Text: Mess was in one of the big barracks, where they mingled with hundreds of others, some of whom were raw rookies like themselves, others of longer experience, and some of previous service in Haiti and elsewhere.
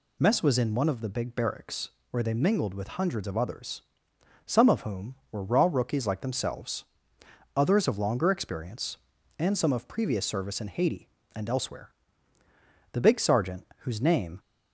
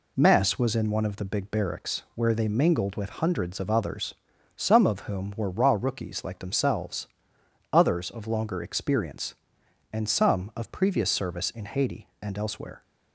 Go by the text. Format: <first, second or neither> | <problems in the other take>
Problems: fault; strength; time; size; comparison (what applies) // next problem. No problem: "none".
second | goes on to say "The big sergeant whose name"; from 12.9 s on; 1.4 s long